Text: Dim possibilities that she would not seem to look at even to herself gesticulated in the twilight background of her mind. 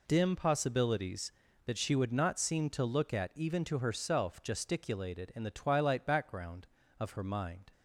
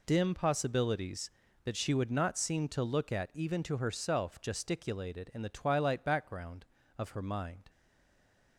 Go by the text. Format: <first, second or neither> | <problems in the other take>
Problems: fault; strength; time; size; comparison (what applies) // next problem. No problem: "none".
first | stays silent after the last word; slight; from 7.6 s on; 0.9 s long